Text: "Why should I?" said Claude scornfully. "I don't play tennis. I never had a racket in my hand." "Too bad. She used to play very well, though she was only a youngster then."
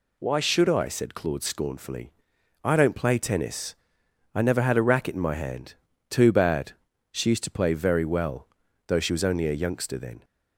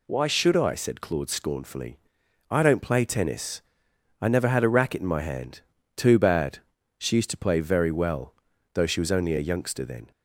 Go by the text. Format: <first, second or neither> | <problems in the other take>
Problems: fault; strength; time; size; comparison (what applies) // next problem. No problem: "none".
neither | none